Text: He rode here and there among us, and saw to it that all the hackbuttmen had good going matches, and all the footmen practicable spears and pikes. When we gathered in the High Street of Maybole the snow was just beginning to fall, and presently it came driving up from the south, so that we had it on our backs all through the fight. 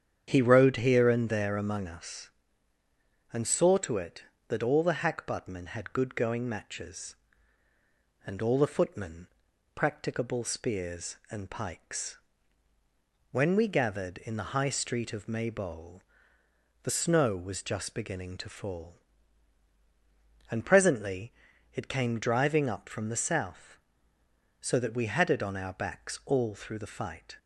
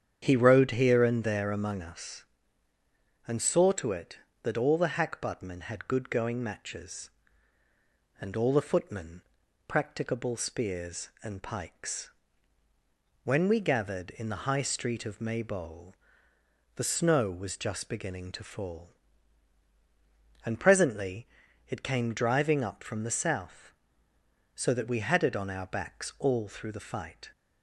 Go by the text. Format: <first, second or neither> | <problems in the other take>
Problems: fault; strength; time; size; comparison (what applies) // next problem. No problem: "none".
neither | starts louder than the rest; strong; the same in both // pauses between "footmen" and "practicable"; noticeable; the same in both // pauses between "Maybole" and "the"; noticeable; the same in both // pauses between "presently" and "it"; the same in both